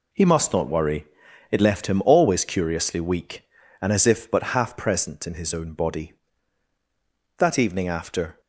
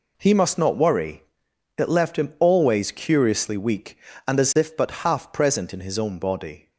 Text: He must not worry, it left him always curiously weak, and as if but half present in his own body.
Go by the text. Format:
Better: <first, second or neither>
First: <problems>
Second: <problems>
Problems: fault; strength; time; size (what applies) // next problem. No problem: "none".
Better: second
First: goes on to say "That evening after"; noticeable; from 7.3 s on; 1.0 s long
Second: none